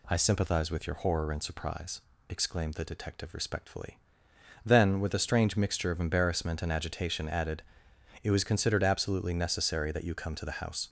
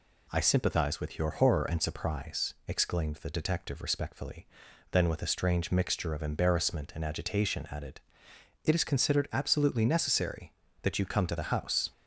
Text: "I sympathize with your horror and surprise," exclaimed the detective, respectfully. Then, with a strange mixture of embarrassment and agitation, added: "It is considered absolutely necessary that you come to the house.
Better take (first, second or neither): second